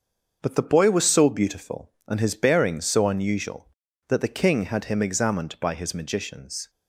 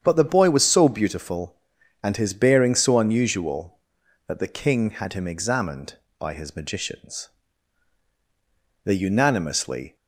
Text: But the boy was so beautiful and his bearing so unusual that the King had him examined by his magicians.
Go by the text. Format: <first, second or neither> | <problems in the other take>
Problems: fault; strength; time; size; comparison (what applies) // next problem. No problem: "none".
first | starts louder than the rest; strong; until 1.0 s; 8.5 dB; also in the first // goes on to say "They unanimously"; noticeable; from 8.8 s on; 1.1 s long